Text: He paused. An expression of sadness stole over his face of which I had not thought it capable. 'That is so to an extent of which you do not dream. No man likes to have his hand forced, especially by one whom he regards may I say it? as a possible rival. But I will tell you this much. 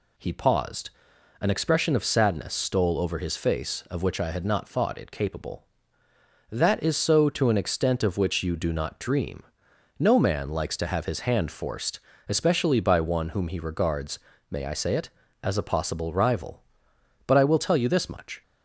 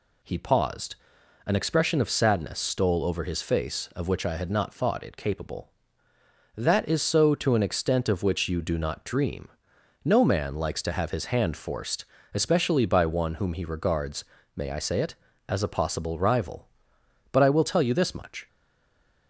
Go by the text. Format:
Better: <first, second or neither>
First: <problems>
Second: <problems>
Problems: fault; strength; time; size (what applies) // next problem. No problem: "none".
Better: first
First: pauses between "regards" and "may"; slight; at 14.1 s; 0.32 s long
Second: pauses between "regards" and "may"; slight; at 14.2 s; 0.32 s long // stays silent after the last word; slight; from 18.4 s on; 0.8 s long